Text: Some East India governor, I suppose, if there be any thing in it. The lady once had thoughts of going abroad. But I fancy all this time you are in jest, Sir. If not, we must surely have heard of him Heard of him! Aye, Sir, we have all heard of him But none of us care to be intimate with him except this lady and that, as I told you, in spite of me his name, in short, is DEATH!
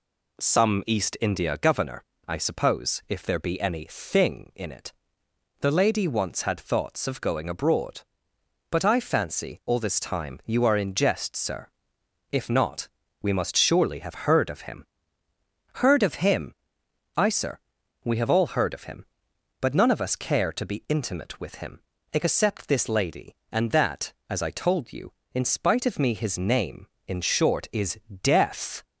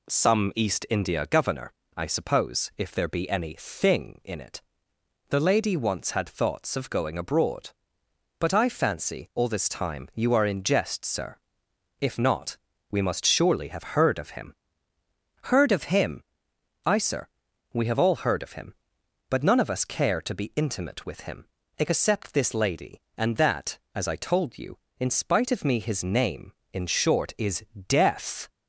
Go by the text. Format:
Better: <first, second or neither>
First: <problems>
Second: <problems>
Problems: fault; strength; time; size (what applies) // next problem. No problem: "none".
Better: neither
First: pauses between "him" and "Heard"; noticeable; at 14.8 s; 0.92 s long // pauses between "him" and "except"; slight; at 21.7 s; 0.32 s long // pauses between "is" and "DEATH"; slight; at 27.9 s; 0.24 s long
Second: pauses between "him" and "Heard"; noticeable; at 14.5 s; 0.92 s long // pauses between "him" and "except"; slight; at 21.4 s; 0.32 s long // pauses between "is" and "DEATH"; slight; at 27.6 s; 0.24 s long